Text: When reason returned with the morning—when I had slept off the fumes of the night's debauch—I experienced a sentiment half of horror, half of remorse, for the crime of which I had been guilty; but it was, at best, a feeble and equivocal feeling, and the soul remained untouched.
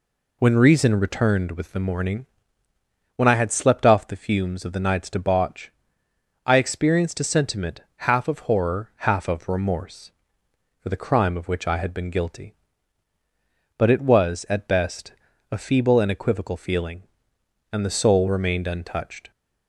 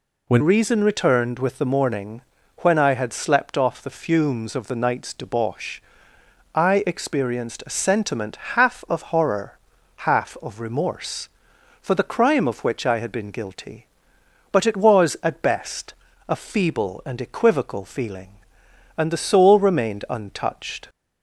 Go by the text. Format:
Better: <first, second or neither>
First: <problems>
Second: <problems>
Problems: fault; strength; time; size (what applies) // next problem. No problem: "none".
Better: first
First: none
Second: changes voice at "reason"; from 0.3 s on; 20.5 s long // pauses between "sentiment" and "half"; slight; at 8.3 s; 0.16 s long